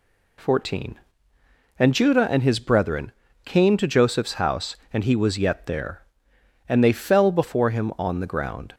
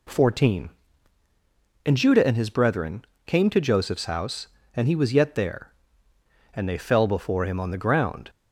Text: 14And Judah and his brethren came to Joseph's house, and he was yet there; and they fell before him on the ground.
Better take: neither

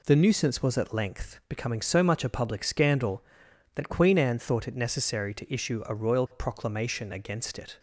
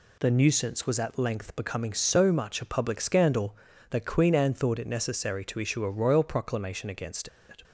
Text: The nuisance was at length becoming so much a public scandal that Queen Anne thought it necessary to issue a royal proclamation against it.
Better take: first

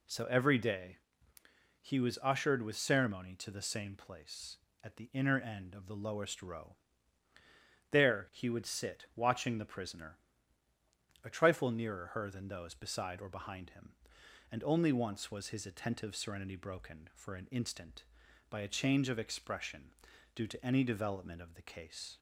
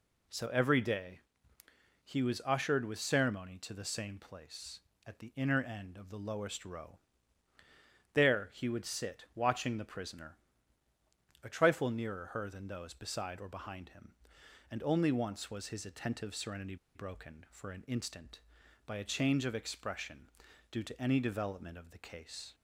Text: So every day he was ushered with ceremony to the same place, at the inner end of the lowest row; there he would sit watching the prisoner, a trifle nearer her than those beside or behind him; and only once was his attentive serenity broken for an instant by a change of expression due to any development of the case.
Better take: first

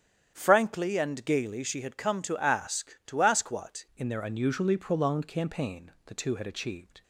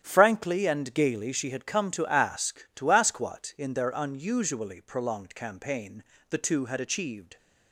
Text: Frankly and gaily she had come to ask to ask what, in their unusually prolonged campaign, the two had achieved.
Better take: second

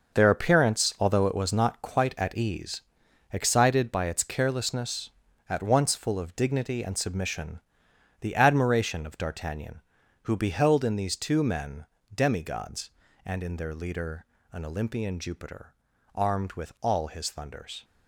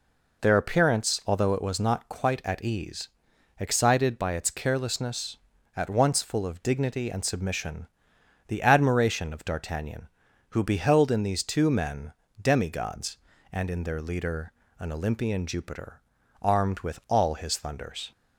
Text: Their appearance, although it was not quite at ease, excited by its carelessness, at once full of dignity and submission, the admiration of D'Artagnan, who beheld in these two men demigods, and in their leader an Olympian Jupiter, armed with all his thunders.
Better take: second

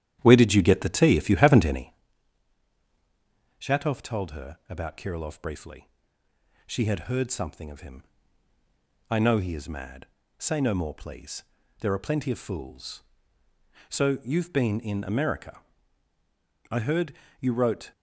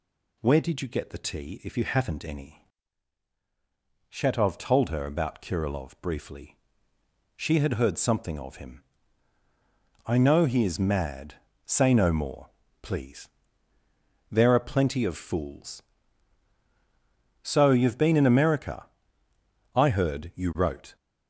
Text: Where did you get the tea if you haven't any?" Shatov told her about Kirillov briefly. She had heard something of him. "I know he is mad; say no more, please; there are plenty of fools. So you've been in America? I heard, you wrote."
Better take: second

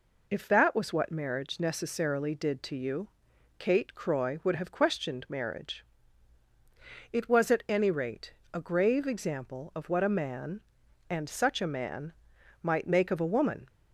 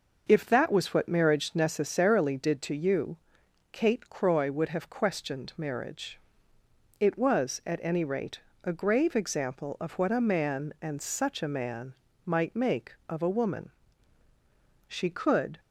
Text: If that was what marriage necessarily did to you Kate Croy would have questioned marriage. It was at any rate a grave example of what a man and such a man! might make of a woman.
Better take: first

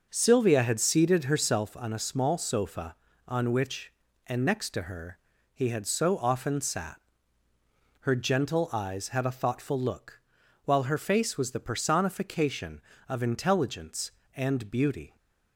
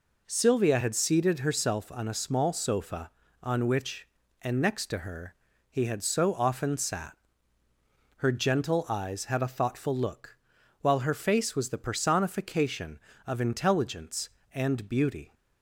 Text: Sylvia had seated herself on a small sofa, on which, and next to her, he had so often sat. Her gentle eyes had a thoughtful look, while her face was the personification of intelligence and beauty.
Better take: second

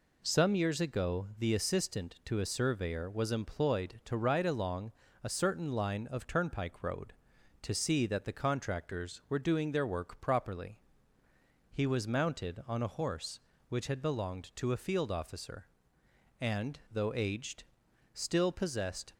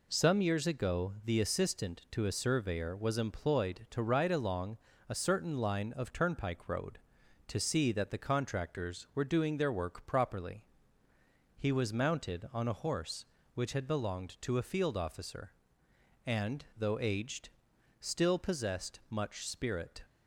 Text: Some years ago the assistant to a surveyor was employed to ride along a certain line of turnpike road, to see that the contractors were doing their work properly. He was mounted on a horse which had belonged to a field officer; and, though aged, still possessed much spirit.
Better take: second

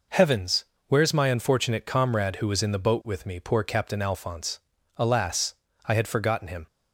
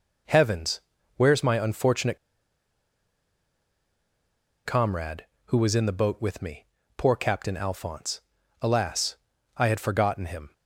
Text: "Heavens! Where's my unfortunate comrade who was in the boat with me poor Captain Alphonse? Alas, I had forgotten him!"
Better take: first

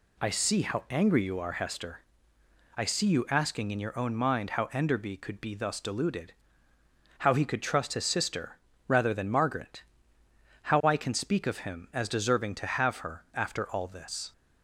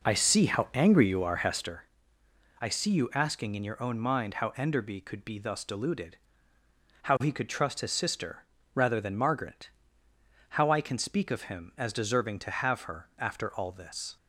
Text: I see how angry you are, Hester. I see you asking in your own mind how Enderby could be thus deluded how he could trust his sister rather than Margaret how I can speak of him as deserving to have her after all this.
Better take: first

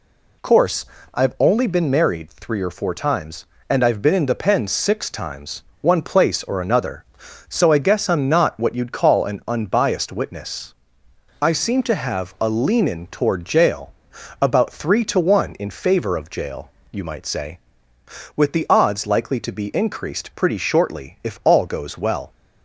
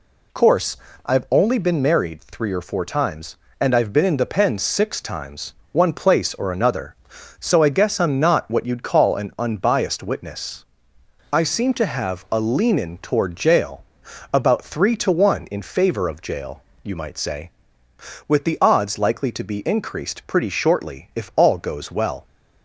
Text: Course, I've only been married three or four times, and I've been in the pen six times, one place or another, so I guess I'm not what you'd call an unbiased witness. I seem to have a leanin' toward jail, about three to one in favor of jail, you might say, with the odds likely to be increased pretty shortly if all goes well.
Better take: neither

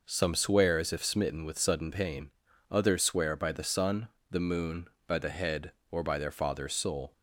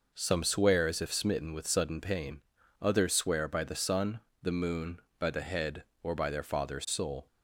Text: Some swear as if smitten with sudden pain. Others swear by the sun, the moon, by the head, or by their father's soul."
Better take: neither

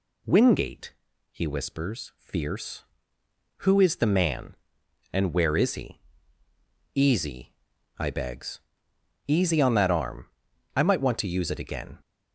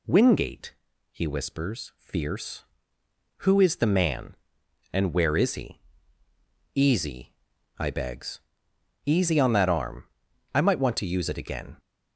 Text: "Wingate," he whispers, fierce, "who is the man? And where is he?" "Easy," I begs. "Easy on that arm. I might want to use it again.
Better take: neither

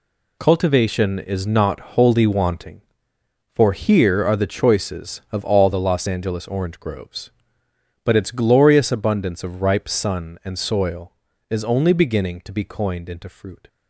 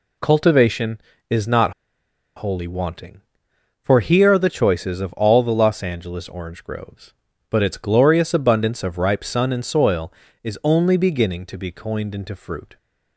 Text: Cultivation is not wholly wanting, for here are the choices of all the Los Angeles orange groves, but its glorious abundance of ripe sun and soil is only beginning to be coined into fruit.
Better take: first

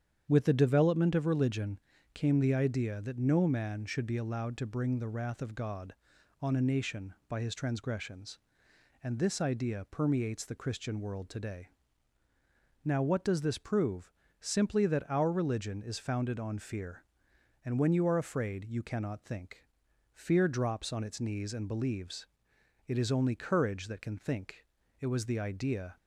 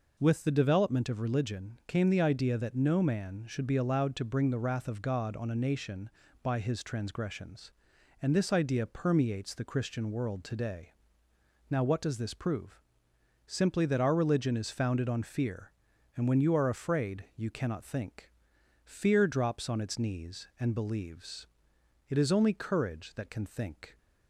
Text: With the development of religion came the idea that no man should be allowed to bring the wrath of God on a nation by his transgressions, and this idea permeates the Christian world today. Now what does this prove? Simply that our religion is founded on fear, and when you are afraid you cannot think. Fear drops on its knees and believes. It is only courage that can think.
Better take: second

